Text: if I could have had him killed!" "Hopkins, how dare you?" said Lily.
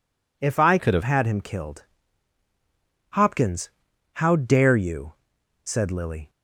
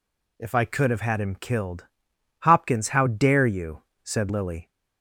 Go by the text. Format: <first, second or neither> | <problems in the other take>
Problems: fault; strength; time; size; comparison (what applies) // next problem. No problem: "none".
second | changes voice from "could" to "have"; from 0.7 to 1.0 s; 0.3 s long